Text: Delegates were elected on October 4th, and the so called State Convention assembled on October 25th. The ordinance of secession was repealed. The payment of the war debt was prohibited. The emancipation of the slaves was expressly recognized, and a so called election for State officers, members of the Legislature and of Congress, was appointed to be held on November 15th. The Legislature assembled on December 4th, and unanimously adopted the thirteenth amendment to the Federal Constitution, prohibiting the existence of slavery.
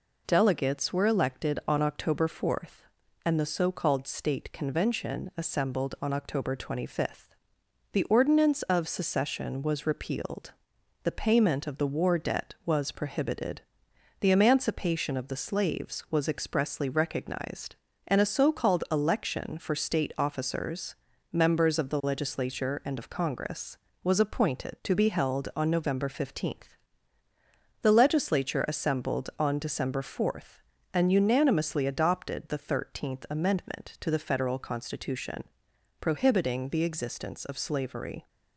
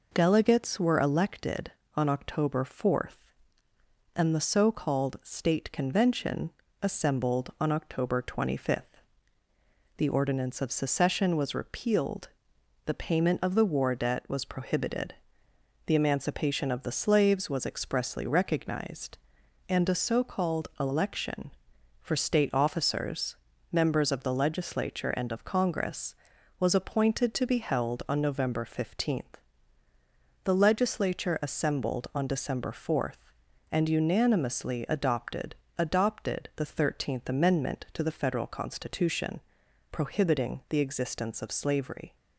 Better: first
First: none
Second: pauses between "Convention" and "assembled"; slight; at 6.5 s; 0.32 s long // says "adopted" twice; at 35.7 s

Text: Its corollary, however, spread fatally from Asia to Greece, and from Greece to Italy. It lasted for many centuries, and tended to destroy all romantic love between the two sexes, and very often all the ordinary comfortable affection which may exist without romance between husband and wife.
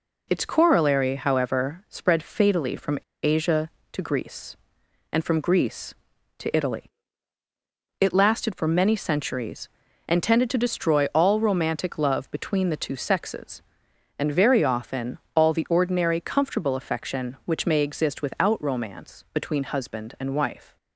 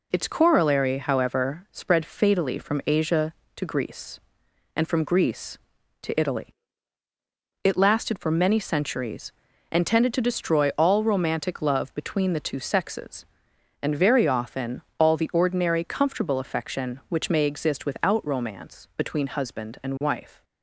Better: second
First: pauses between "from" and "Asia"; slight; at 2.9 s; 0.25 s long // pauses between "often" and "all"; slight; at 15.1 s; 0.16 s long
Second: pauses between "often" and "all"; slight; at 14.8 s; 0.16 s long

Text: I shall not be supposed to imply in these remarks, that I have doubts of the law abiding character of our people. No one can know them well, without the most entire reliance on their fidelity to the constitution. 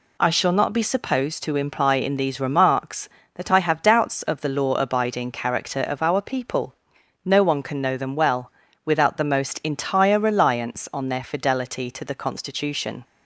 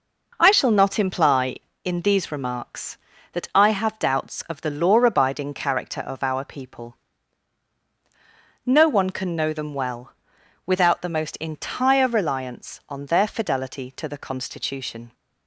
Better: first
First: none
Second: skips "be supposed to"; at 0.9 s

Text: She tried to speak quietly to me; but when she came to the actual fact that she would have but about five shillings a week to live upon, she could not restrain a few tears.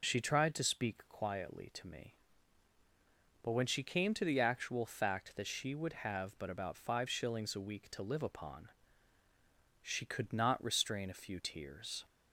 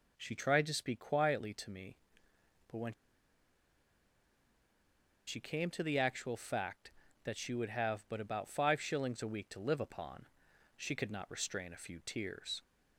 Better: first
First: none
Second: pauses between "when" and "she"; strong; at 2.9 s; 2.3 s long

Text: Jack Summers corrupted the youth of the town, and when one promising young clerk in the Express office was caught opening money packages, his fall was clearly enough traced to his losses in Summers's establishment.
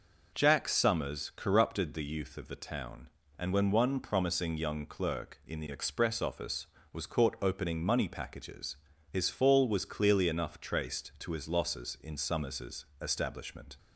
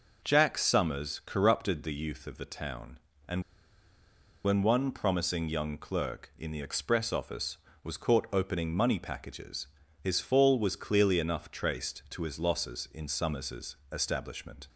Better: first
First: none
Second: pauses between "and" and "when"; at 3.4 s; 1.0 s long

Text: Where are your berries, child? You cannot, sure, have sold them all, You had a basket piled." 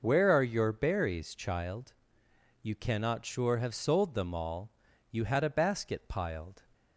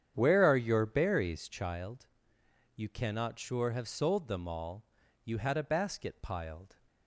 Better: first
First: none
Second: starts louder than the rest; strong; until 1.7 s; 9 dB

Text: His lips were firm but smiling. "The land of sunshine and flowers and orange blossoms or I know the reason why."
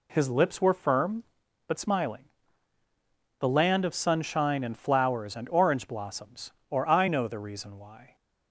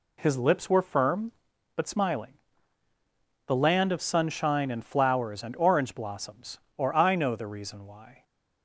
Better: neither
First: none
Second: none

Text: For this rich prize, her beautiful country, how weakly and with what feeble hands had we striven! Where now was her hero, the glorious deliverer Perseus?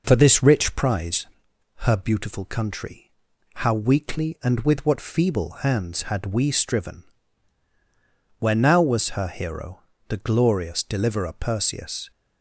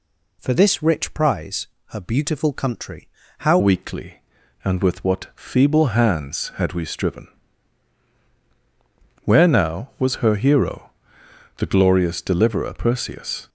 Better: first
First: none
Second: changes voice at "weakly"; from 3.5 s on; 9.9 s long

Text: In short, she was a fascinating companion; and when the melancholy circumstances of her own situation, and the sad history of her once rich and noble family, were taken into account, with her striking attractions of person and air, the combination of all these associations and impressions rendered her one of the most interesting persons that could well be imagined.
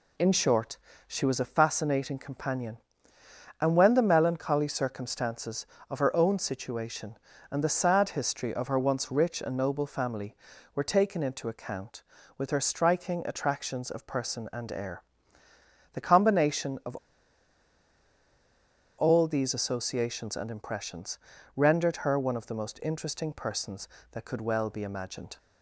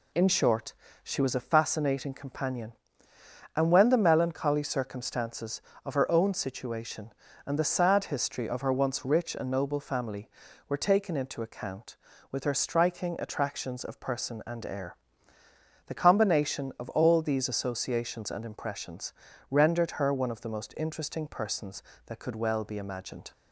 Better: second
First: pauses between "of" and "all"; strong; at 16.9 s; 2.0 s long // pauses between "impressions" and "rendered"; at 21.1 s; 0.38 s long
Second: pauses between "impressions" and "rendered"; at 19.1 s; 0.38 s long

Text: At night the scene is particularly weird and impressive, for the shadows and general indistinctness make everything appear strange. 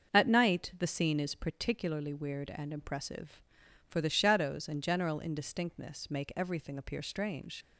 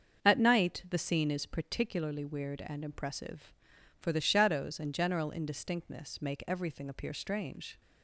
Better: second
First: starts louder than the rest; until 1.1 s; 6.5 dB // leaves "strange" unfinished; at 7.6 s; 75 ms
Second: starts louder than the rest; until 1.2 s; 7 dB

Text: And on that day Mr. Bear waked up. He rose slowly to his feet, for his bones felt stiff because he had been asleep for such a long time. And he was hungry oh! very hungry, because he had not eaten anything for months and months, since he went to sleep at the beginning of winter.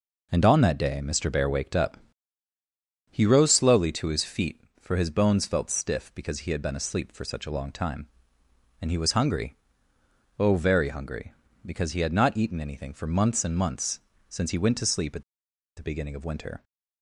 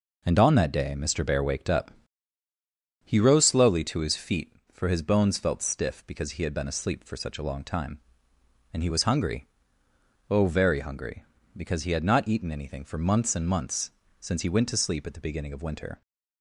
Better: second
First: pauses between "hungry" and "oh"; noticeable; at 9.5 s; 0.84 s long // pauses between "at" and "the"; noticeable; at 15.2 s; 0.54 s long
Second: pauses between "hungry" and "oh"; noticeable; at 9.4 s; 0.84 s long

